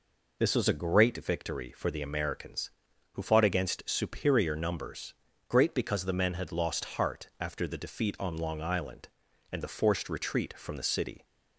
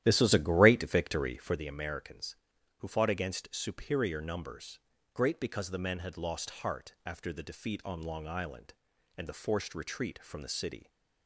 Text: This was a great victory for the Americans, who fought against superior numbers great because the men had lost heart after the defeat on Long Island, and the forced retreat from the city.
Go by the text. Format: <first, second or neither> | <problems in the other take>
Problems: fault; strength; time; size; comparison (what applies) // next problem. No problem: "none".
first | starts louder than the rest; strong; until 1.6 s; 12.5 dB // pauses between "numbers" and "great"; slight; at 4.7 s; 0.34 s long; slight in the first